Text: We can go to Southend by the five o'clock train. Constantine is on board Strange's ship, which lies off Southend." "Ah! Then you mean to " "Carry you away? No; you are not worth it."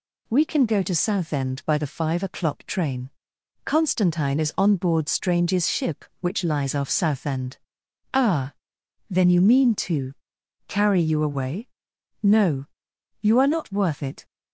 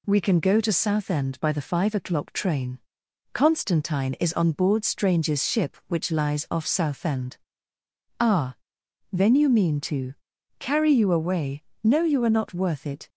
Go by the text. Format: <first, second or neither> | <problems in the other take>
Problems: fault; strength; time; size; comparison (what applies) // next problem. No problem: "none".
neither | none